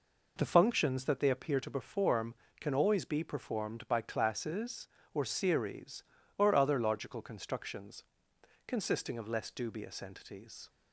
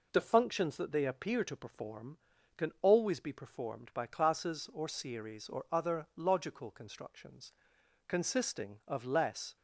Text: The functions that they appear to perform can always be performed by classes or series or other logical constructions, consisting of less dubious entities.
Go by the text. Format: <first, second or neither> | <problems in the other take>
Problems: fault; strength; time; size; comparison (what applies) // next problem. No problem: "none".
first | stops before "dubious entities"; at 9.5 s